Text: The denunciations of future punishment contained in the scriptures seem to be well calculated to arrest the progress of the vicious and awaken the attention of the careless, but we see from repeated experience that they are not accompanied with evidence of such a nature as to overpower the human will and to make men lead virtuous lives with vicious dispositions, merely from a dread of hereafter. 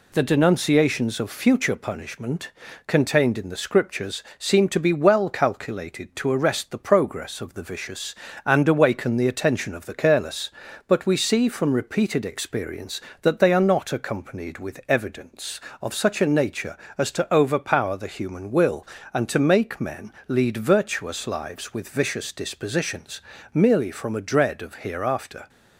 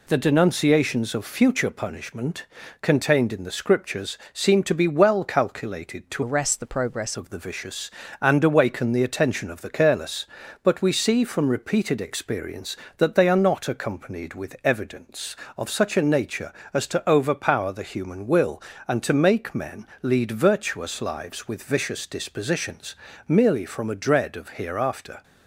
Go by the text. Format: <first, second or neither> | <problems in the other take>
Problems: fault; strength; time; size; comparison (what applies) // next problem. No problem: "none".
first | pauses between "punishment" and "contained"; slight; at 2.4 s; 0.34 s long; slight in the first // pauses between "scriptures" and "seem"; slight; at 4.1 s; 0.16 s long; slight in the first // changes voice from "arrest" to "progress"; from 6.2 to 7.1 s; 0.9 s long // pauses between "men" and "lead"; slight; at 19.8 s; 0.16 s long; slight in the first